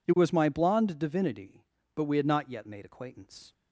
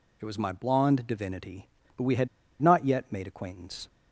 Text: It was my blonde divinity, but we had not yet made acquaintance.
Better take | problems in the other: first | pauses between "had" and "not"; slight; at 2.2 s; 0.33 s long

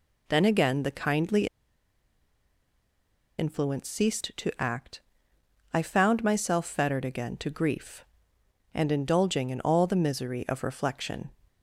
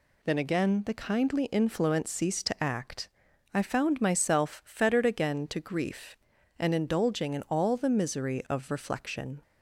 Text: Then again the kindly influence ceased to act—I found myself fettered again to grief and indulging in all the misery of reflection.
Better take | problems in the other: second | pauses between "kindly" and "influence"; strong; at 1.4 s; 1.9 s long

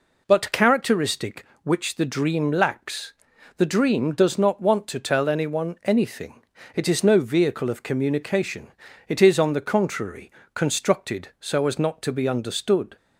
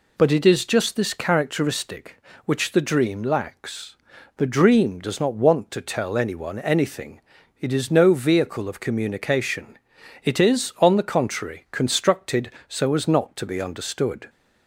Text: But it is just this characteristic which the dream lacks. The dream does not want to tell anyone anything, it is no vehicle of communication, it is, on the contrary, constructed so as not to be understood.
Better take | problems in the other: second | skips "it is just this"; at 0.5 s

